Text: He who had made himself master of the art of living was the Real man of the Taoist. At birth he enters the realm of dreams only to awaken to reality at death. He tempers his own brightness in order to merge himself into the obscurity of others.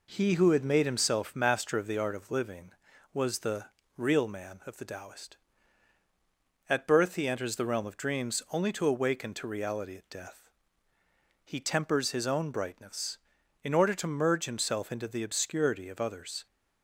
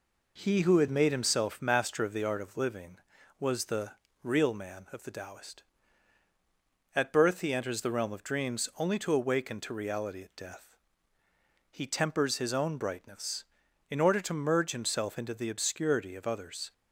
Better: neither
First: pauses between "the" and "Real"; slight; at 3.6 s; 0.28 s long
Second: pauses between "the" and "Real"; slight; at 3.9 s; 0.28 s long

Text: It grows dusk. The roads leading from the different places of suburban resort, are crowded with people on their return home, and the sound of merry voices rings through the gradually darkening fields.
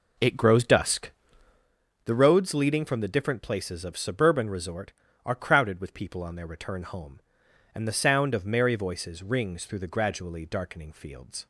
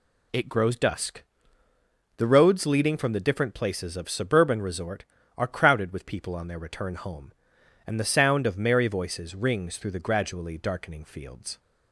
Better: second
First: starts louder than the rest; noticeable; until 1.7 s; 4 dB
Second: none

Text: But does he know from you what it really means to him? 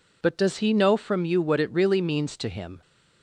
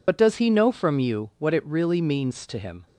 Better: first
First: none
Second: loses the start of "But"; at 0.0 s; 45 ms

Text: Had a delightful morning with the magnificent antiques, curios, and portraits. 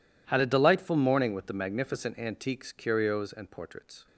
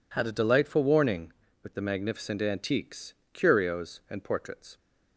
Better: first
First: none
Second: says "warning" for "morning"; at 0.8 s

